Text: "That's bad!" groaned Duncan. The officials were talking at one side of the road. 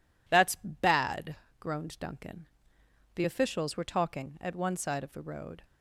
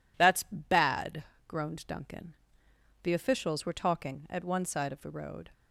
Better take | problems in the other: neither | none

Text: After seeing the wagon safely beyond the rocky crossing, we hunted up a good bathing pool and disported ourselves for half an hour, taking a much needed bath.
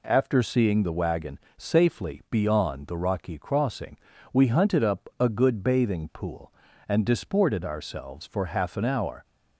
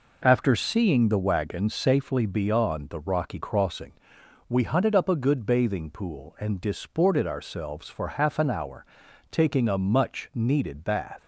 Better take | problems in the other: second | pauses between "wagon" and "safely"; slight; at 1.3 s; 0.18 s long // stops before "taking a much needed bath"; at 9.2 s

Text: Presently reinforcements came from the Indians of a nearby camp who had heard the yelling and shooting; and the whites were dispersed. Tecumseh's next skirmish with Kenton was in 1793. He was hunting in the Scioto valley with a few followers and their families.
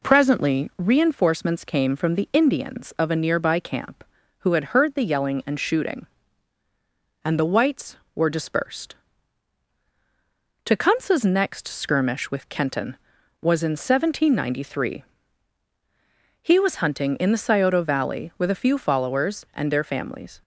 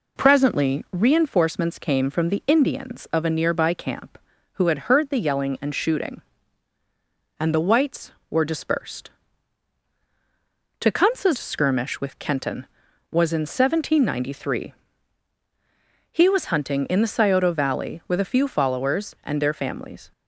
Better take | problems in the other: first | skips "next"; at 11.3 s

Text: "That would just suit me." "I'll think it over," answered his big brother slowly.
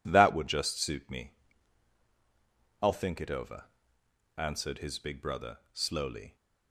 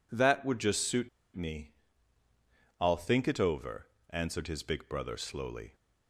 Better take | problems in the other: first | pauses between "suit" and "me"; slight; at 1.0 s; 0.27 s long

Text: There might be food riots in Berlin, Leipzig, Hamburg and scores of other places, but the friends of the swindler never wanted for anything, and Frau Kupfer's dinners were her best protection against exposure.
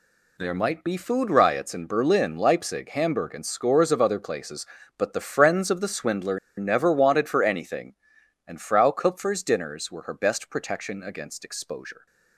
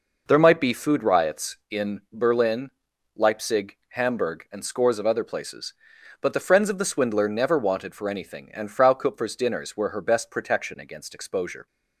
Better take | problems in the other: second | pauses between "swindler" and "never"; slight; at 6.3 s; 0.19 s long

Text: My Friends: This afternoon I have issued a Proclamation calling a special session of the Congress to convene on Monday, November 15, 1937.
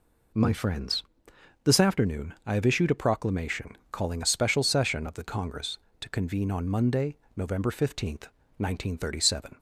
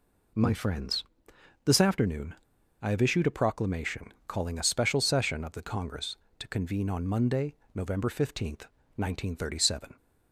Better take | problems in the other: first | pauses between "afternoon" and "I"; noticeable; at 2.3 s; 0.47 s long

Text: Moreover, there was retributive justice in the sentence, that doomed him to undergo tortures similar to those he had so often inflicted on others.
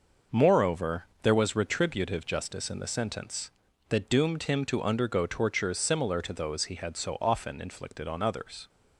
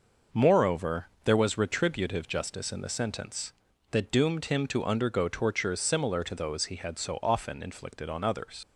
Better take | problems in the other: first | leaves "others" unfinished; at 8.6 s; 65 ms

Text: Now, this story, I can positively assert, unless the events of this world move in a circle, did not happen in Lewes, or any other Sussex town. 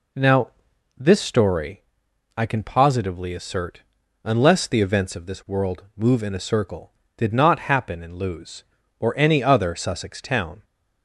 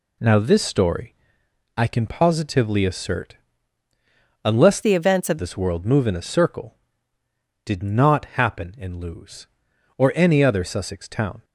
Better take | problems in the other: first | changes voice from "the" to "of"; from 4.8 to 5.3 s; 0.5 s long

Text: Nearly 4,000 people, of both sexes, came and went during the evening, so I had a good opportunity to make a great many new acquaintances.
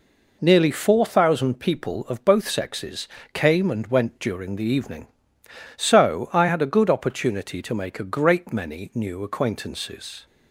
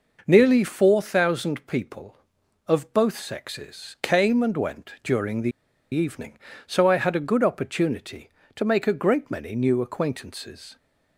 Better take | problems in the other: first | pauses between "the" and "evening"; at 5.5 s; 0.41 s long

